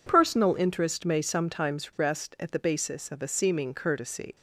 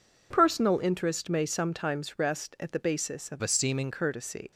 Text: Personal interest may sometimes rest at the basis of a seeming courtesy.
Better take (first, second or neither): first